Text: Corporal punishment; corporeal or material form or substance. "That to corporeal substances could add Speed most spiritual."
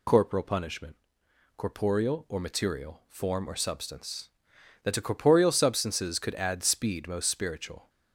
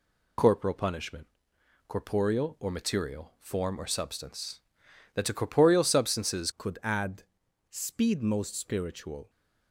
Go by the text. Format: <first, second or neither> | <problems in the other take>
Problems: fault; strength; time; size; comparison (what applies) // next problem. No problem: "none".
first | changes voice at "could"; from 6.5 s on; 2.7 s long // pauses between "add" and "Speed"; noticeable; at 7.2 s; 0.46 s long